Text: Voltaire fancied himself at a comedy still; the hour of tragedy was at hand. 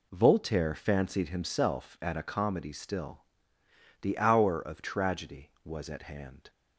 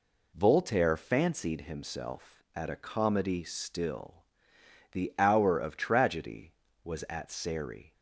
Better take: first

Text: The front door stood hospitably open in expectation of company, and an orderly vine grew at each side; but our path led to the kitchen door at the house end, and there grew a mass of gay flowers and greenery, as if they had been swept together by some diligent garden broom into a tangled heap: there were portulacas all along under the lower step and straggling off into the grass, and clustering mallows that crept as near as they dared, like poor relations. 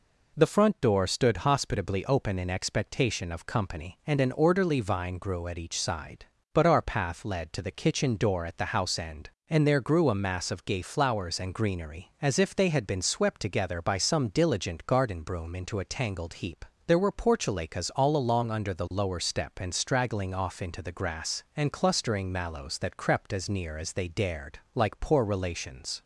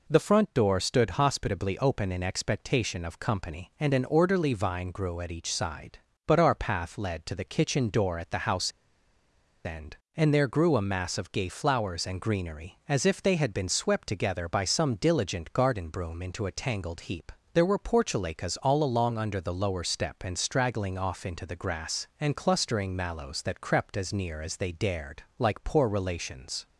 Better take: first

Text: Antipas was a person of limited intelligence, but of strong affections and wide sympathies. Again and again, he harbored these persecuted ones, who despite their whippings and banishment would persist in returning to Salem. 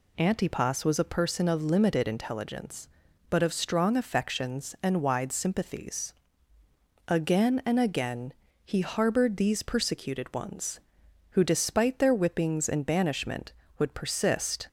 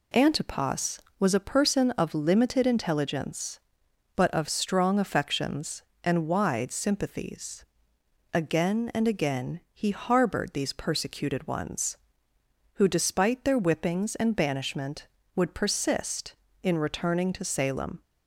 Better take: second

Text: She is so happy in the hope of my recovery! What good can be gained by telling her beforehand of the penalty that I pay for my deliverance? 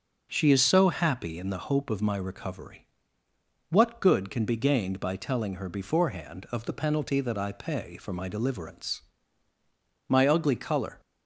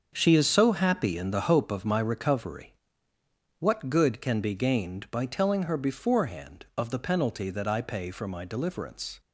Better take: second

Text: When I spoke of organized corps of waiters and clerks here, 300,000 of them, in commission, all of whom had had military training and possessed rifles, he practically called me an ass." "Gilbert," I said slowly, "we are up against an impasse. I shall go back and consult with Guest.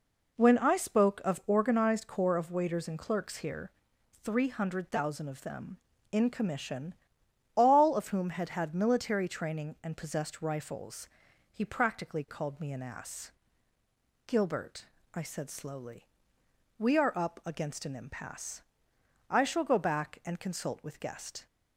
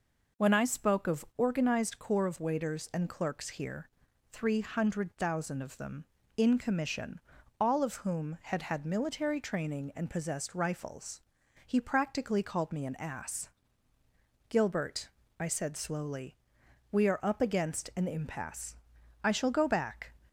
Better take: first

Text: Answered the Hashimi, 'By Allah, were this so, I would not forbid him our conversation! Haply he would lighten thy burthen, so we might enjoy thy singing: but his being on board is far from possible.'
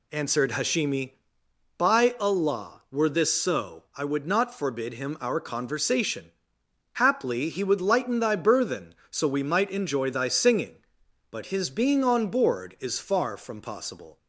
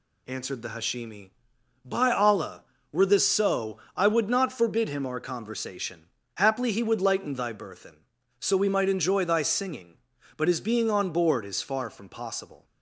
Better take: second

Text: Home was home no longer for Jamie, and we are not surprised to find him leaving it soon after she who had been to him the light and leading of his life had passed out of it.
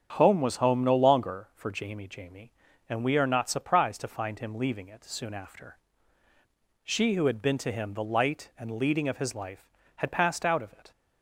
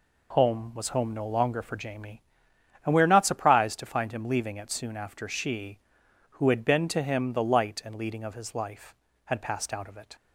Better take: second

